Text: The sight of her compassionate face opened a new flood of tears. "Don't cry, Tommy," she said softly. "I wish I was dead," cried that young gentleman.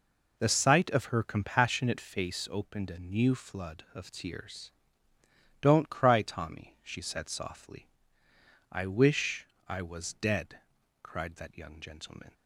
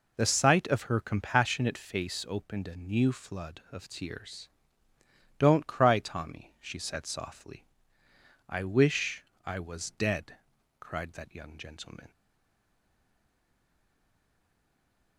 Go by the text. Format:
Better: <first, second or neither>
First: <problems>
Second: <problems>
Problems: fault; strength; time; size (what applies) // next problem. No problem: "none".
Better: first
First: pauses between "wish" and "I"; slight; at 9.4 s; 0.18 s long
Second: pauses between "wish" and "I"; slight; at 9.2 s; 0.18 s long // stays silent after the last word; strong; from 12.1 s on; 3.0 s long